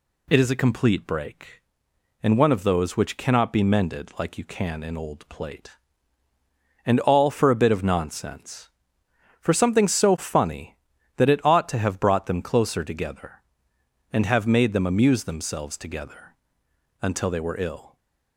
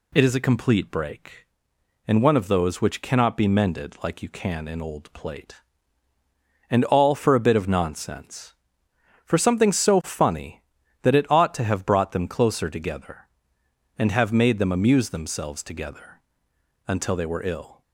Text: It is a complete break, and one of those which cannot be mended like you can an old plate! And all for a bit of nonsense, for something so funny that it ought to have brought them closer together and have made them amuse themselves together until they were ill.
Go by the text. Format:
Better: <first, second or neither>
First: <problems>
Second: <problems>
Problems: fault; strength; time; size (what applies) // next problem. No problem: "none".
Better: neither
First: pauses between "together" and "until"; noticeable; at 16.3 s; 0.66 s long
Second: pauses between "together" and "until"; noticeable; at 16.2 s; 0.66 s long